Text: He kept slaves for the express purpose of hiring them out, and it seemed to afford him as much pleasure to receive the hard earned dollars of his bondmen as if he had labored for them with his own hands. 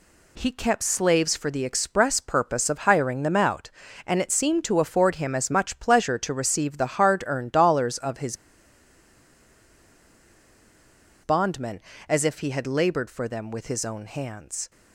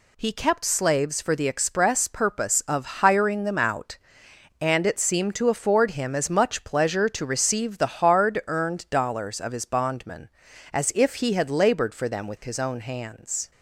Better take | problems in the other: second | pauses between "his" and "bondmen"; strong; at 8.3 s; 2.8 s long

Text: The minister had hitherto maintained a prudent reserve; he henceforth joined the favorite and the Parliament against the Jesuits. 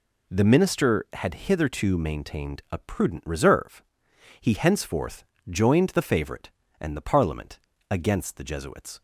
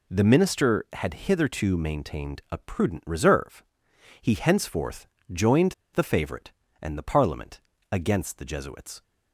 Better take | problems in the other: first | pauses between "henceforth" and "joined"; slight; at 5.0 s; 0.24 s long; slight in the first // pauses between "joined" and "the"; slight; at 5.7 s; 0.21 s long // pauses between "Parliament" and "against"; slight; at 7.6 s; 0.32 s long; slight in the first

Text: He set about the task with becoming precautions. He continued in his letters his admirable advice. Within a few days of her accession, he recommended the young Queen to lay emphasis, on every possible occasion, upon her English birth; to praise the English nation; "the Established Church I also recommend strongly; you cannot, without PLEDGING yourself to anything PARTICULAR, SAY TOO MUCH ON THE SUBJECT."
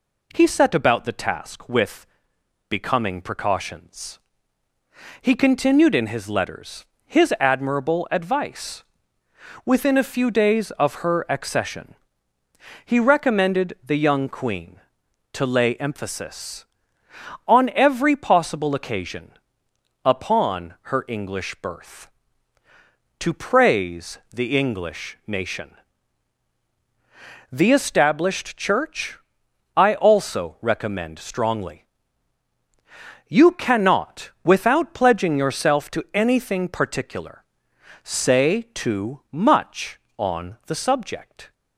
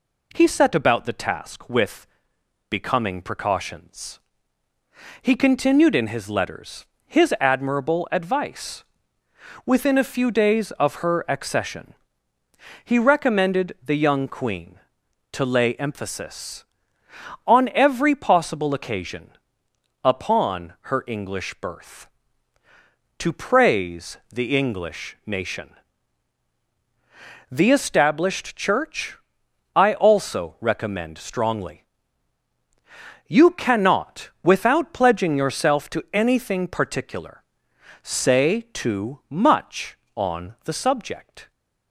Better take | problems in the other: neither | pauses between "with" and "becoming"; noticeable; the same in both // pauses between "letters" and "his"; slight; the same in both // pauses between "Church" and "I"; noticeable; the same in both

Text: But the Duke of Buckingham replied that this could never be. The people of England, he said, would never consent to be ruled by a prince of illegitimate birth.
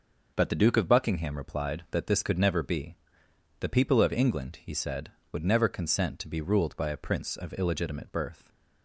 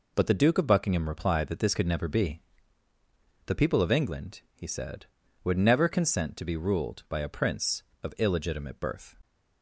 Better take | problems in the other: neither | none

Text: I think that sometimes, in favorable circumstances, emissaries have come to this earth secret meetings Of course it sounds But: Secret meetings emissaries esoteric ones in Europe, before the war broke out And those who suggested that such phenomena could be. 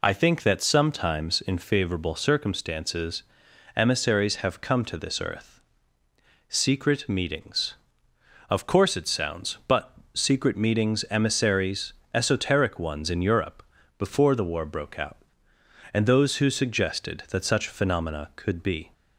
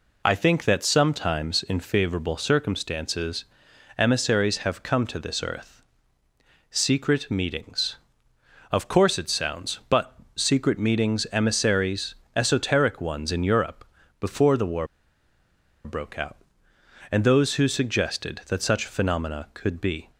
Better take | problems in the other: first | pauses between "earth" and "secret"; noticeable; at 5.7 s; 0.96 s long; noticeable in the first // pauses between "emissaries" and "esoteric"; slight; at 12.1 s; 0.20 s long; slight in the first // pauses between "war" and "broke"; at 14.8 s; 0.99 s long

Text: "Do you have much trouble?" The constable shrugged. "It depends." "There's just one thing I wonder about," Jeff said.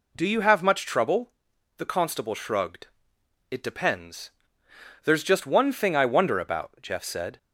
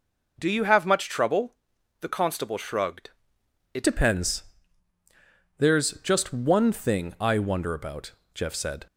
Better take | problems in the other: first | changes voice at "depends"; from 3.8 s on; 5.0 s long

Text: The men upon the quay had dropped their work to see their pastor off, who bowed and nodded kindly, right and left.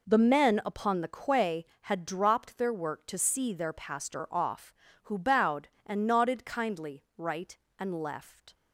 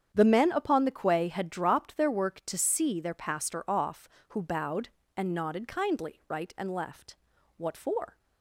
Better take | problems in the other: first | starts louder than the rest; strong; until 1.1 s; 8.5 dB // goes on to say "What for"; noticeable; from 7.5 s on; 0.62 s long

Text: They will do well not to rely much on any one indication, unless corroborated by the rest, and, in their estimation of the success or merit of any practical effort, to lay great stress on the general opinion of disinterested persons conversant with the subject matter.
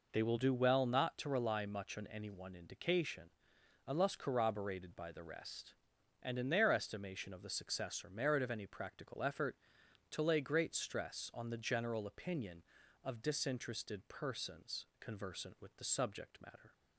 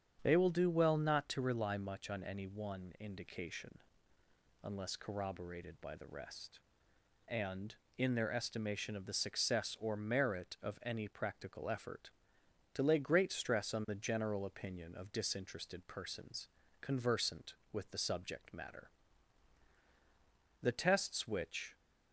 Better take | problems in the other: first | starts louder than the rest; strong; until 1.2 s; 8 dB // pauses between "persons" and "conversant"; slight; at 16.4 s; 0.34 s long // goes on to say "The tests which"; noticeable; from 20.6 s on; 1.1 s long

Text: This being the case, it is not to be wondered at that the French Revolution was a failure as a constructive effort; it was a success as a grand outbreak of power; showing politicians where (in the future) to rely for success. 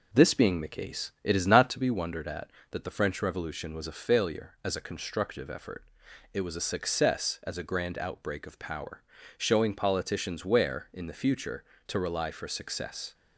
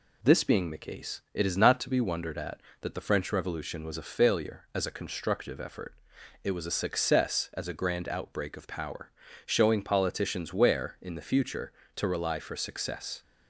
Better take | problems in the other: second | starts louder than the rest; noticeable; until 1.9 s; 5 dB

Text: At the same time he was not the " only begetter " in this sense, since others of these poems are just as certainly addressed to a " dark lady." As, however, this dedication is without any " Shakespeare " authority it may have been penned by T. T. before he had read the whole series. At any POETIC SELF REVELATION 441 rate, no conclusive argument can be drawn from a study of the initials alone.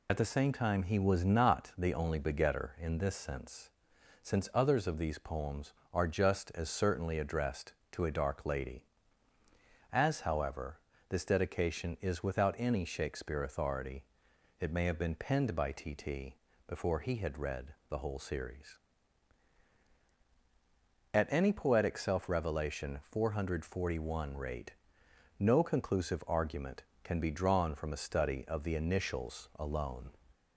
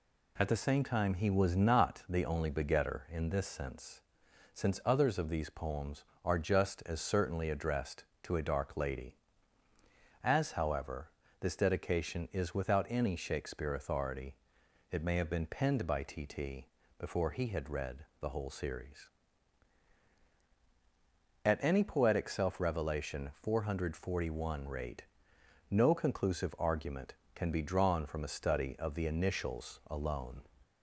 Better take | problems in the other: second | loses the start of "At"; at 0.0 s; 55 ms // pauses between "authority" and "it"; noticeable; at 14.0 s; 0.56 s long; noticeable in the second // pauses between "T" and "before"; slight; at 16.3 s; 0.32 s long; slight in the second // pauses between "read" and "the"; slight; at 17.7 s; 0.16 s long; slight in the second

